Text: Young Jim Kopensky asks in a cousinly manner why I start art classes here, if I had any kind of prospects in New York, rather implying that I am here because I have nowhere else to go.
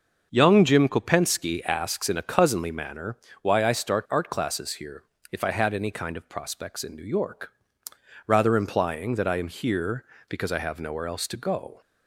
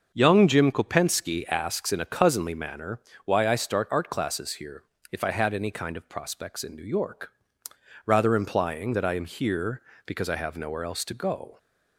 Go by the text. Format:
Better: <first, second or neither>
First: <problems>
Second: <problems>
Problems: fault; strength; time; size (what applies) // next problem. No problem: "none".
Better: neither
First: starts louder than the rest; until 1.3 s; 6.5 dB // pauses between "manner" and "why"; slight; at 3.1 s; 0.28 s long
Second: starts louder than the rest; until 1.1 s; 6.5 dB // pauses between "manner" and "why"; slight; at 2.9 s; 0.28 s long